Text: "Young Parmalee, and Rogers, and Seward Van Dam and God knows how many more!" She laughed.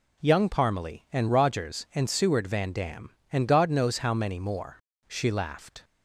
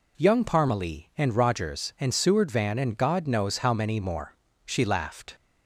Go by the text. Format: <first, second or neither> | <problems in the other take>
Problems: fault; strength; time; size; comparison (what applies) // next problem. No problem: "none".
first | skips "Dam"; at 2.7 s